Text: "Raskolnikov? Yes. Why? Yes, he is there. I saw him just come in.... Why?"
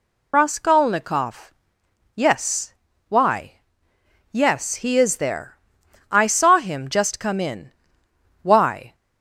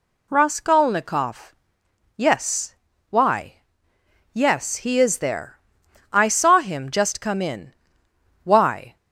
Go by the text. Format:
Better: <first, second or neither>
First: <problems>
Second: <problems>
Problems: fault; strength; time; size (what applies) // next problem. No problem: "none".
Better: second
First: loses the start of "Raskolnikov"; at 0.3 s; 50 ms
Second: none